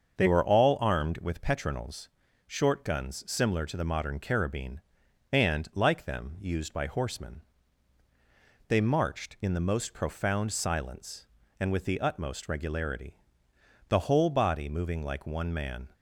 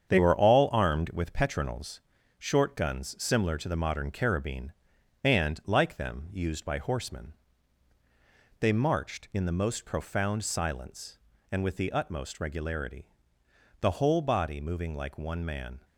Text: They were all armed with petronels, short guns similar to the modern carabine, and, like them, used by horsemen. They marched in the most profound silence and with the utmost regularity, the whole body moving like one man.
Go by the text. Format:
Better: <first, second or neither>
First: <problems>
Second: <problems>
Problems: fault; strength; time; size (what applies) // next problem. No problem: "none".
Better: first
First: starts louder than the rest; until 1.1 s; 6.5 dB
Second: gets quieter; throughout; 6.5 dB // starts louder than the rest; strong; until 1.1 s; 8 dB